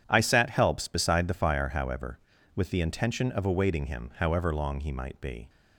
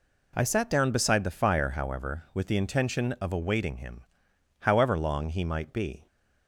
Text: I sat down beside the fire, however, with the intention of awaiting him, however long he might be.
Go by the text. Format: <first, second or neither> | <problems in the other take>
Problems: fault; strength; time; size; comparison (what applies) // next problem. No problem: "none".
second | starts louder than the rest; strong; until 1.0 s; 9 dB // says "helps" for "down"; at 0.5 s